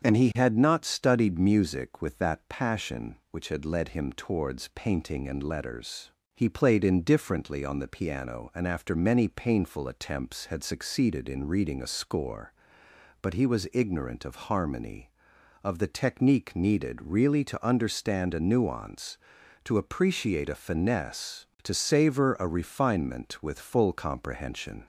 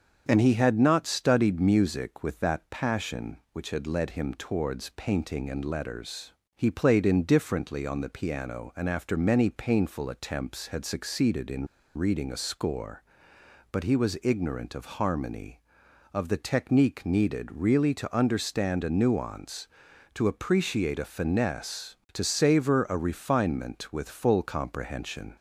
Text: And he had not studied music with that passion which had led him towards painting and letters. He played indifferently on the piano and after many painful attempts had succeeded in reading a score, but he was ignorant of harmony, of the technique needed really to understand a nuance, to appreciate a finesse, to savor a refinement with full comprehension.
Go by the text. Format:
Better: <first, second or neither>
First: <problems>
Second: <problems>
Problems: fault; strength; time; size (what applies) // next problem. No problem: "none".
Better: first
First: starts louder than the rest; strong; until 1.0 s; 7 dB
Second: starts louder than the rest; until 1.3 s; 7 dB // pauses between "in" and "reading"; slight; at 11.6 s; 0.30 s long